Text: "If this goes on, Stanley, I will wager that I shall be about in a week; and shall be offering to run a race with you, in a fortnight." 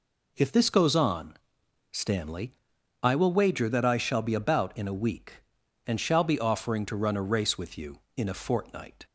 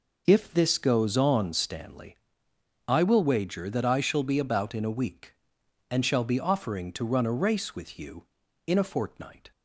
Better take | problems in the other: neither | none

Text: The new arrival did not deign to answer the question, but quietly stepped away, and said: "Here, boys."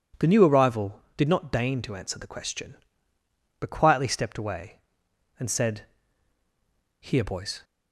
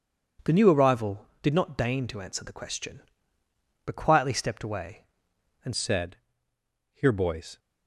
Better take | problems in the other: first | changes voice at "said"; from 5.7 s on; 1.8 s long

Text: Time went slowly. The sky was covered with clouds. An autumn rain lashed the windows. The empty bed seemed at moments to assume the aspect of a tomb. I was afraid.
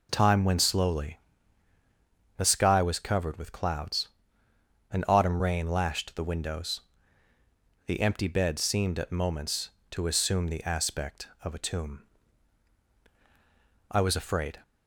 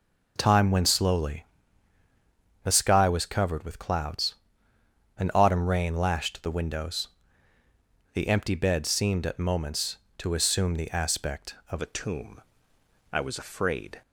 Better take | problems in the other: first | changes voice at "a"; from 11.8 s on; 2.2 s long

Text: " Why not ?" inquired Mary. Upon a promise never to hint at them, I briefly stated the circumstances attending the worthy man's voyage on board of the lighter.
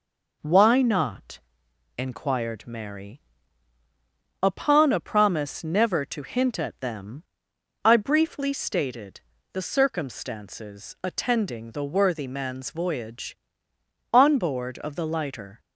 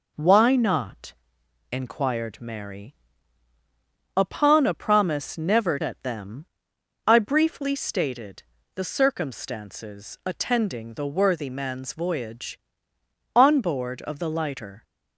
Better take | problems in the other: first | skips "to hint"; at 5.7 s // pauses between "stated" and "the"; slight; at 8.4 s; 0.32 s long; slight in the first

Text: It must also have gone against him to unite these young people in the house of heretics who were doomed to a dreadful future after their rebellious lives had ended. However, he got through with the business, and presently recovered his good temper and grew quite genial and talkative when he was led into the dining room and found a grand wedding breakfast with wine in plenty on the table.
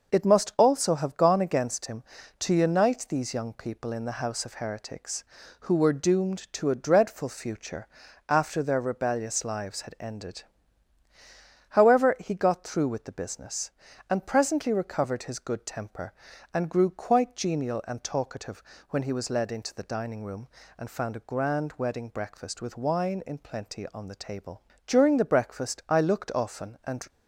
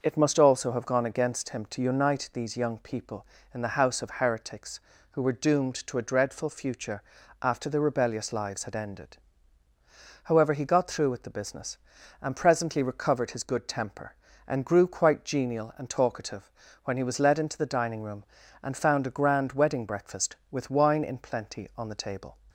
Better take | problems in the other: second | pauses between "future" and "after"; at 7.8 s; 0.40 s long; also in the second // pauses between "talkative" and "when"; slight; at 18.6 s; 0.28 s long; slight in the second // goes on to say "During the breakfast I looked often and"; strong; from 24.8 s on; 2.2 s long

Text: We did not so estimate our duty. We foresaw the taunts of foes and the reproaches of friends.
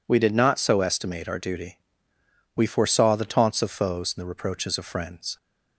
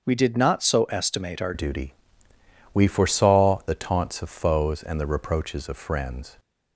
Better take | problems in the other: first | starts louder than the rest; until 1.0 s; 6.5 dB // changes voice at "duty"; from 1.5 s on; 4.8 s long

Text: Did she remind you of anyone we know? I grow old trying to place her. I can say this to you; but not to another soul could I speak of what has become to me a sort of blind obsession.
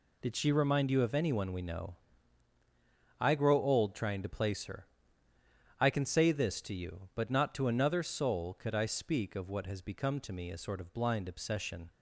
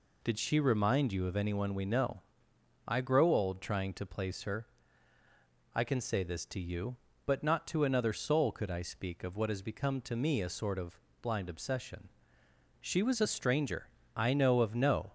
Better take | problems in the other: first | pauses between "of" and "blind"; slight; at 10.9 s; 0.24 s long // goes on to say "She was a stranger I know of no"; strong; from 12.8 s on; 2.3 s long

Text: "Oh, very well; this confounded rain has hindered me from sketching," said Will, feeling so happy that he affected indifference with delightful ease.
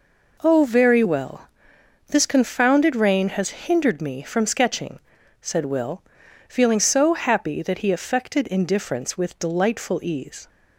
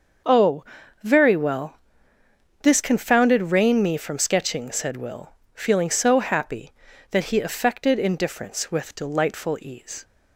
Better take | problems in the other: first | starts louder than the rest; until 1.6 s; 6.5 dB // skips "has hindered"; at 3.8 s

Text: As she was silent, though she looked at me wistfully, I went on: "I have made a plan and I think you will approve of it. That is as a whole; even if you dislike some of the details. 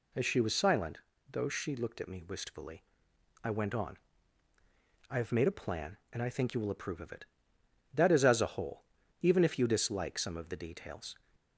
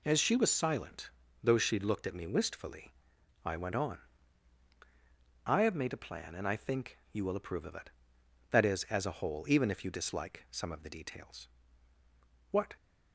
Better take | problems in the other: first | goes on to say "What"; slight; from 12.4 s on; 0.26 s long

